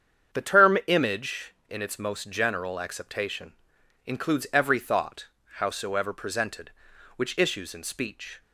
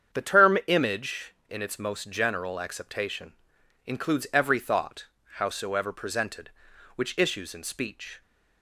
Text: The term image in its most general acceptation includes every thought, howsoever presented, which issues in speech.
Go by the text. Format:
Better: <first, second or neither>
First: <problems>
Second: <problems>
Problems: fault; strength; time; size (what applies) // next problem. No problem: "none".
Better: neither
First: starts louder than the rest; strong; until 1.4 s; 7.5 dB // pauses between "acceptation" and "includes"; noticeable; at 3.5 s; 0.54 s long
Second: starts louder than the rest; strong; until 1.2 s; 7.5 dB // pauses between "acceptation" and "includes"; noticeable; at 3.3 s; 0.54 s long